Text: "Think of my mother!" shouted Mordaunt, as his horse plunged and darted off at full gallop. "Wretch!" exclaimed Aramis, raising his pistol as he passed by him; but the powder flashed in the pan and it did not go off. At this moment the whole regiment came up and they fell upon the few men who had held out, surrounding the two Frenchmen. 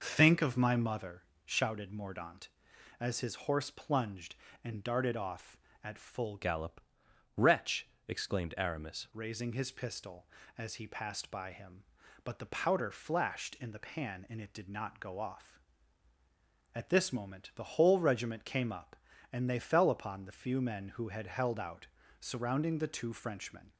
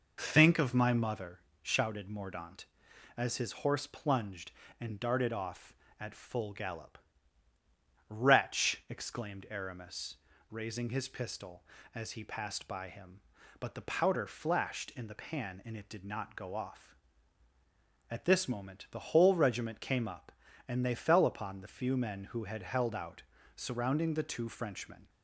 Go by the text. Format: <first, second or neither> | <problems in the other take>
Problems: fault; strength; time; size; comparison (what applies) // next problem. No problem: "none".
second | changes voice from "gallop" to "Aramis"; from 6.3 to 9.0 s; 2.7 s long